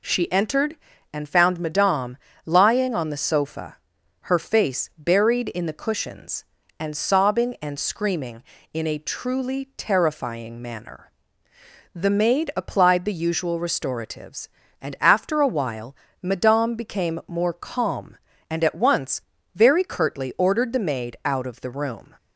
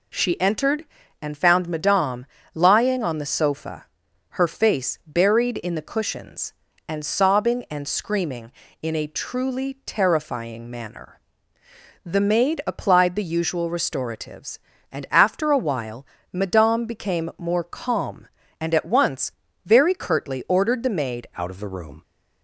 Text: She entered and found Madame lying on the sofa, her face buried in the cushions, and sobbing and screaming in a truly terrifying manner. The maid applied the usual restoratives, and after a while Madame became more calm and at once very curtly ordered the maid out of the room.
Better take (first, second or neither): first